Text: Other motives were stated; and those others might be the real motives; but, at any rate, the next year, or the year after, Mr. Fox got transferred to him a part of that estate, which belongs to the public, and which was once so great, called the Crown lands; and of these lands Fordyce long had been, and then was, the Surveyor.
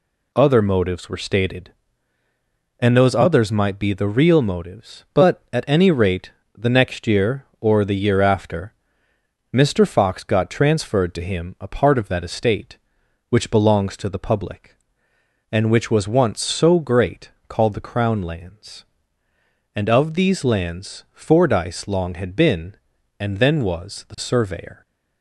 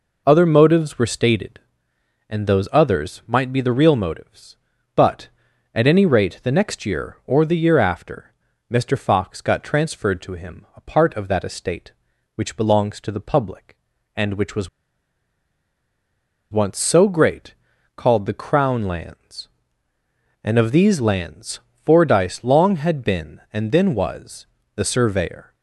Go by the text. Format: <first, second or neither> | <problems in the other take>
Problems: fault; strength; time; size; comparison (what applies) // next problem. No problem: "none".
first | pauses between "was" and "once"; strong; at 14.6 s; 1.8 s long // pauses between "lands" and "Fordyce"; slight; at 21.5 s; 0.26 s long